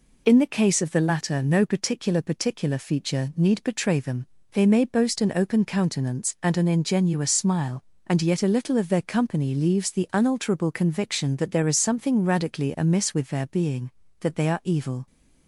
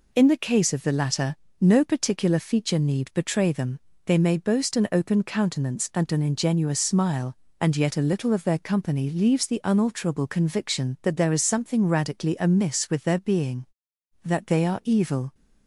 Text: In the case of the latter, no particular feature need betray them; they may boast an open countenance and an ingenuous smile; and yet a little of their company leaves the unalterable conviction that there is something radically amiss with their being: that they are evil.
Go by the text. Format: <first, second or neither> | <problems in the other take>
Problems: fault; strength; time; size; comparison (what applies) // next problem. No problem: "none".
second | says "particular" twice; at 2.2 s